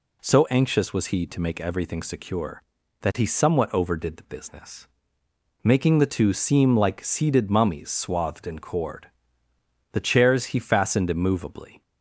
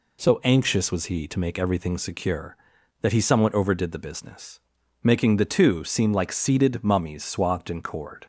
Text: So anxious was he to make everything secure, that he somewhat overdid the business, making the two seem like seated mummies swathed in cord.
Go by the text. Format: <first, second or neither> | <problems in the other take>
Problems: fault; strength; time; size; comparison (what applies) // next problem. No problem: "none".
second | goes on to say "The chairs he fastened immovably"; strong; from 9.9 s on; 1.9 s long